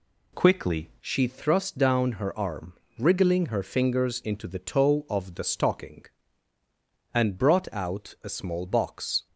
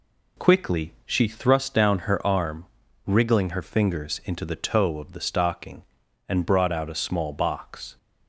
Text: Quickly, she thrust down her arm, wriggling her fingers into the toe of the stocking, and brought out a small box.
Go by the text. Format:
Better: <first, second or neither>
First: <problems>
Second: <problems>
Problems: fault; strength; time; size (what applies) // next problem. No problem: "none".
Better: second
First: changes voice at "she"; from 1.0 s on; 8.2 s long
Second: none